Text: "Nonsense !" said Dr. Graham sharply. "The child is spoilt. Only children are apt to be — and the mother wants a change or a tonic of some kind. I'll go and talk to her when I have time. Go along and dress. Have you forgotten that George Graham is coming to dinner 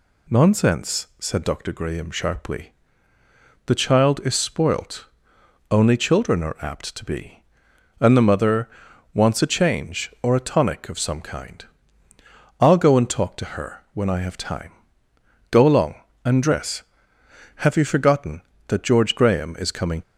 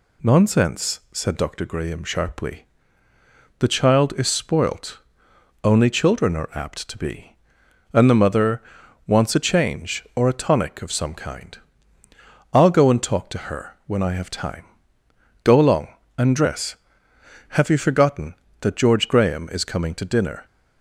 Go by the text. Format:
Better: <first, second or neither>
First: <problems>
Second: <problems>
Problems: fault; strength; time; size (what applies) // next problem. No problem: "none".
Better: second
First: pauses between "mother" and "wants"; noticeable; at 8.6 s; 0.46 s long // stops before "to dinner"; at 20.0 s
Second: pauses between "mother" and "wants"; noticeable; at 8.6 s; 0.46 s long